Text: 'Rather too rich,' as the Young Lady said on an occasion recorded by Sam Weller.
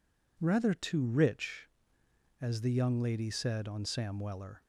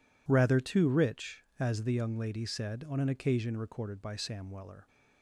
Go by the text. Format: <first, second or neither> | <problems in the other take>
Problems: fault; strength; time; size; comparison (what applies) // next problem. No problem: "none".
second | skips "an occasion recorded by"; at 3.8 s